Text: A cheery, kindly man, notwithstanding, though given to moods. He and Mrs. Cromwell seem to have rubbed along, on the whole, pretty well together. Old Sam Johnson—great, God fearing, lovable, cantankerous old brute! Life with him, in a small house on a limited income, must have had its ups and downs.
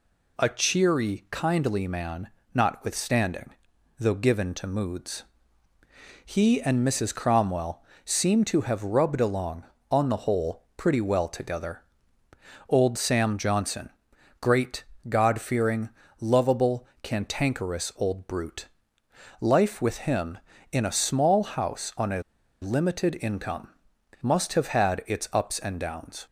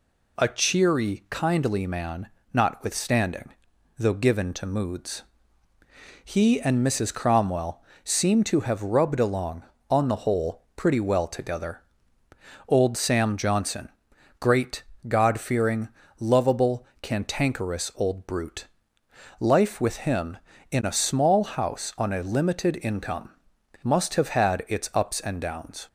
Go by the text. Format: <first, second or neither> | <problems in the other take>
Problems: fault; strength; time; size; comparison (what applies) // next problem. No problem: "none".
second | pauses between "Cromwell" and "seem"; slight; at 7.8 s; 0.22 s long; slight in the second // pauses between "a" and "limited"; at 22.2 s; 0.41 s long